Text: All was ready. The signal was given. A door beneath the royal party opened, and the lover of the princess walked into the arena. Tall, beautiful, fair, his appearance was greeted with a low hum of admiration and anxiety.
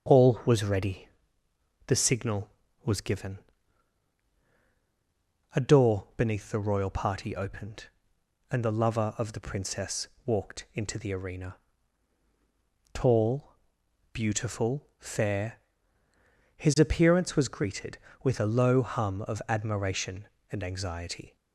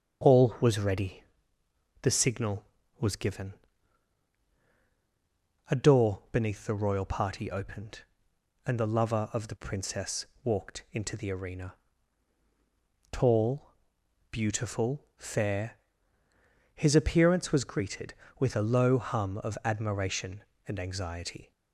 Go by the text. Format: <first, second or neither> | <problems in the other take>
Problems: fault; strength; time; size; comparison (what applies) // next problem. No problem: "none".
neither | starts louder than the rest; the same in both // pauses between "princess" and "walked"; slight; the same in both